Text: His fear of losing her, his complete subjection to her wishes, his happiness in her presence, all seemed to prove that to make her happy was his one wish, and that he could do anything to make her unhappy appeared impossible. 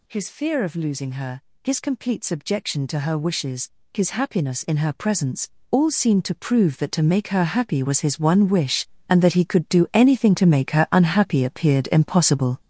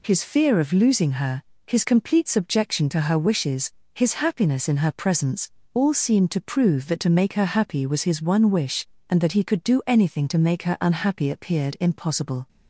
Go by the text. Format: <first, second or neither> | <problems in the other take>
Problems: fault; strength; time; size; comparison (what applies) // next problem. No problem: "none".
second | gets louder; strong; throughout; 8 dB